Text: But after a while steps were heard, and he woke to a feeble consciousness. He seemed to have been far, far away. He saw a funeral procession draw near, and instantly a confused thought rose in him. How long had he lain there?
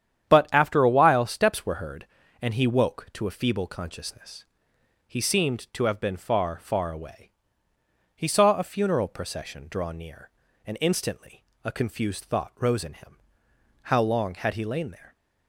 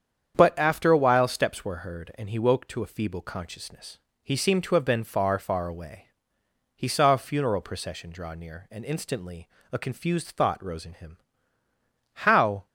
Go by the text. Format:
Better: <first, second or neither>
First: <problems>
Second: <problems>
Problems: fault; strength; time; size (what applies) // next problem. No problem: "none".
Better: first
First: starts louder than the rest; strong; until 1.3 s; 9.5 dB // pauses between "instantly" and "a"; slight; at 11.4 s; 0.20 s long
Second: starts louder than the rest; strong; until 1.4 s; 8 dB // pauses between "instantly" and "a"; slight; at 9.4 s; 0.24 s long // stops before "long had he lain there"; at 12.6 s